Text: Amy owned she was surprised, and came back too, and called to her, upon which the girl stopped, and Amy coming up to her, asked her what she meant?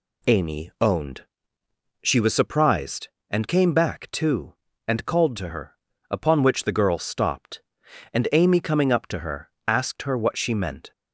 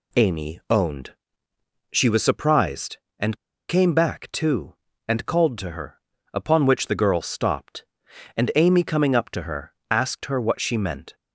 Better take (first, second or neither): first